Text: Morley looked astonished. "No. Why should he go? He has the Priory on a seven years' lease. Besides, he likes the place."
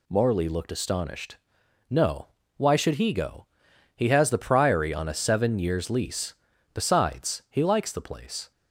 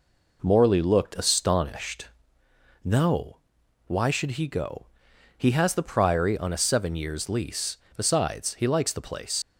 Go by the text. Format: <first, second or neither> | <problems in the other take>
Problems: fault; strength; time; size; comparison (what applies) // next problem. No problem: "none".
first | leaves "place" unfinished; at 9.4 s; 85 ms